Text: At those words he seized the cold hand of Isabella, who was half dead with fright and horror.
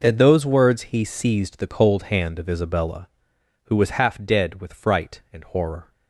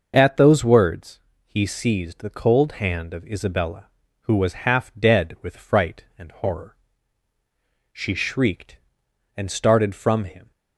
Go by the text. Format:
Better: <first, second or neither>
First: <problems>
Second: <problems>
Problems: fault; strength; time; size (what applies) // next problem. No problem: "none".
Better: first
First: none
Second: pauses between "words" and "he"; slight; at 1.1 s; 0.26 s long // goes on to say "She shrieked and started from him"; strong; from 7.9 s on; 2.5 s long